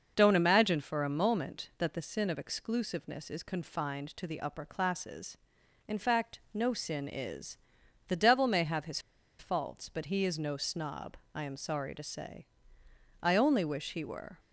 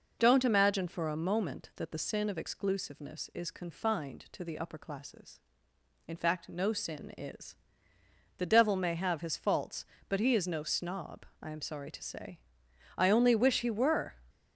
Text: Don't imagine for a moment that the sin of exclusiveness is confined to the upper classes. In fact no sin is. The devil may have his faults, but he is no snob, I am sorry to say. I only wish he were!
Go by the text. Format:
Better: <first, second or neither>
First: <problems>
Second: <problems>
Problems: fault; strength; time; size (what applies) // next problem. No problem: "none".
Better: second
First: starts louder than the rest; noticeable; until 1.1 s; 6 dB // pauses between "his" and "faults"; at 8.9 s; 0.40 s long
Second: none